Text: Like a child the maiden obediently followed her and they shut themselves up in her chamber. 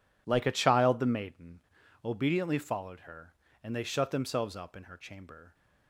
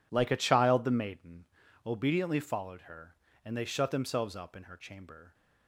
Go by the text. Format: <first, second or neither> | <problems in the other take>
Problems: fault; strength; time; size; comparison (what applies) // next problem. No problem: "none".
neither | pauses between "maiden" and "obediently"; the same in both